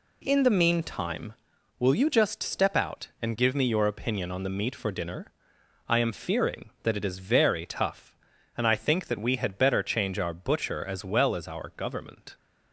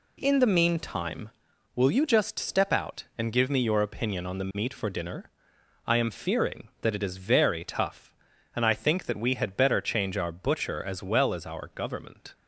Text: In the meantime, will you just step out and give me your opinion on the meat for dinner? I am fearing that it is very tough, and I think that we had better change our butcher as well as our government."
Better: neither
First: none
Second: none

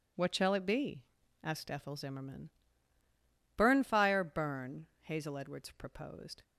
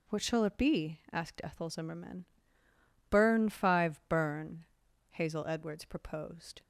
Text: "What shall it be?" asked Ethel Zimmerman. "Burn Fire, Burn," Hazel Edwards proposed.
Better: first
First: none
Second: says "Five" for "Fire"; at 3.4 s

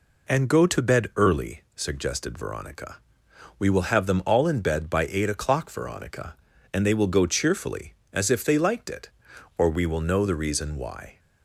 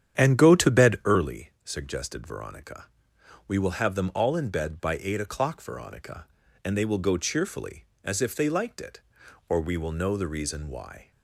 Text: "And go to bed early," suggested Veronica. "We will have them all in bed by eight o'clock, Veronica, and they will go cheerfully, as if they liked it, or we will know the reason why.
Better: first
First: none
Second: starts louder than the rest; strong; until 1.2 s; 9.5 dB

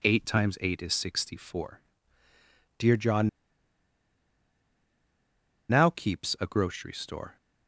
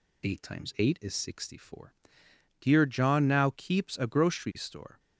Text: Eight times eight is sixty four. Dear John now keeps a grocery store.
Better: second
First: pauses between "John" and "now"; strong; at 3.2 s; 2.4 s long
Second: none

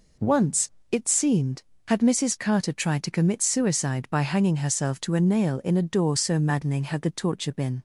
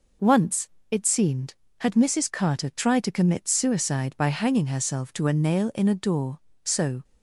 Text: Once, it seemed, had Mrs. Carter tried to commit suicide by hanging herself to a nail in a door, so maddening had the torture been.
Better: first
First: none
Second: stops before "maddening had the torture been"; at 7.0 s

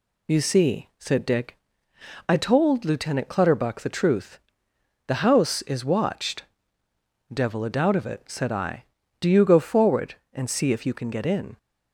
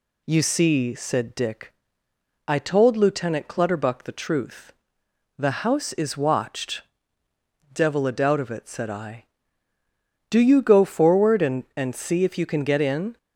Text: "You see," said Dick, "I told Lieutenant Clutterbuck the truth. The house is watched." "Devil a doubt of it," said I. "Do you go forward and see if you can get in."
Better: first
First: none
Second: says "and" twice; at 11.7 s

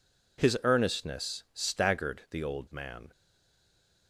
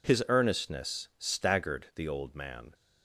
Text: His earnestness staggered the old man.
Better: second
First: stays silent after the last word; slight; from 3.1 s on; 0.9 s long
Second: none

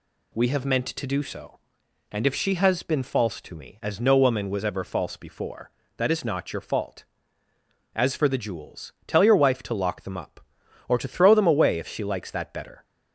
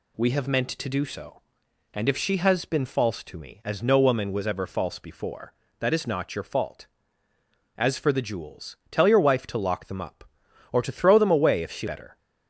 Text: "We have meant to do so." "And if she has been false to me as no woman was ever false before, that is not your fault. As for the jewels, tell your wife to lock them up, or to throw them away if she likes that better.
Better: first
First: none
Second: skips "likes that"; at 11.8 s

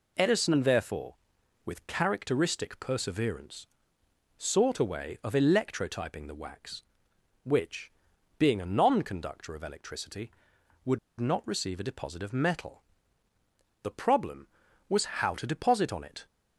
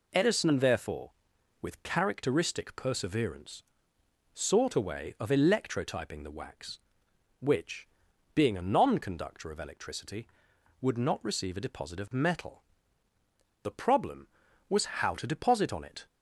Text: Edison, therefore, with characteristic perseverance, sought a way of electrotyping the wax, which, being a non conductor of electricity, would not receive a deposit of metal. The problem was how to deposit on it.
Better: second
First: pauses between "would" and "not"; slight; at 10.9 s; 0.21 s long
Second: none

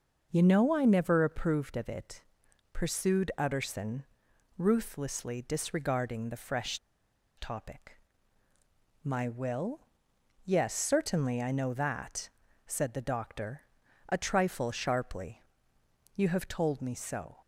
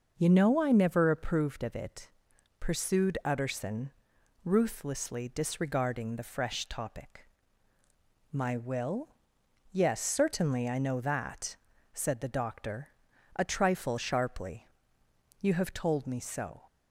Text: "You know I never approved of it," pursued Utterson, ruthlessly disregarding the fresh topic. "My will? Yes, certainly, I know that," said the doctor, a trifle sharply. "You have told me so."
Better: second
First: starts louder than the rest; noticeable; until 1.3 s; 6 dB // pauses between "fresh" and "topic"; noticeable; at 6.7 s; 0.59 s long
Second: starts louder than the rest; noticeable; until 1.1 s; 6 dB

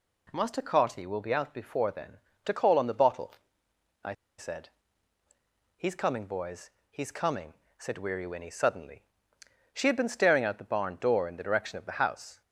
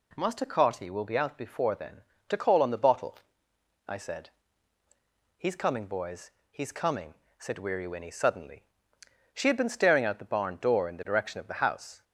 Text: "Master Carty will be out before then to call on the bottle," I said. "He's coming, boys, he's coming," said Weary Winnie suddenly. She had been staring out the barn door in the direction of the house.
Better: second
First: pauses between "I" and "said"; slight; at 4.1 s; 0.26 s long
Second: none

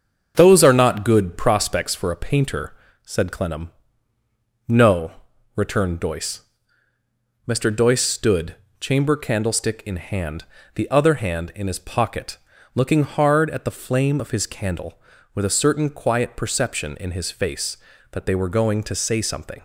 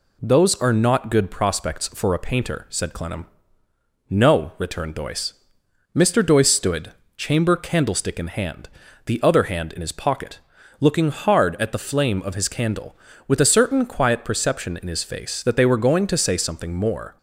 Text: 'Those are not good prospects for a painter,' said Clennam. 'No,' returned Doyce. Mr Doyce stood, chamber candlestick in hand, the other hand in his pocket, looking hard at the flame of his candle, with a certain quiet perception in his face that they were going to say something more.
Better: second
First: starts louder than the rest; until 1.3 s; 7 dB // stops before "more"; at 19.5 s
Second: none

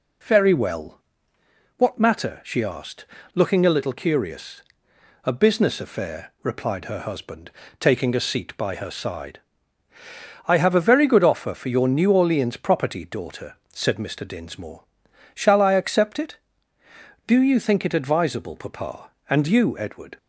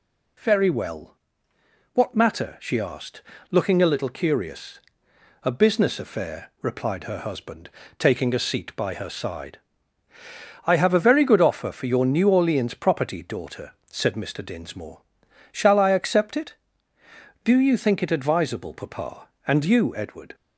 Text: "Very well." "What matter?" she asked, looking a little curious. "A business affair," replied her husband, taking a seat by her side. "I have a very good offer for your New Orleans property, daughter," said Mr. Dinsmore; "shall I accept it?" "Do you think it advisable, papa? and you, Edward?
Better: second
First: starts louder than the rest; slight; until 1.4 s; 2.5 dB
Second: none

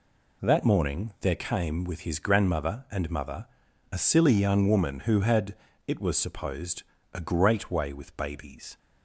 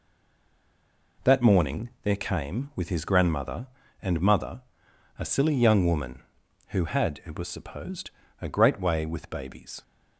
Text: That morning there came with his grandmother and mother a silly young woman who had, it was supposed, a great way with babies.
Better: first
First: pauses between "mother" and "a"; noticeable; at 3.4 s; 0.46 s long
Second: stays silent before the first word; noticeable; until 1.1 s; 1.1 s long // pauses between "mother" and "a"; noticeable; at 4.6 s; 0.56 s long

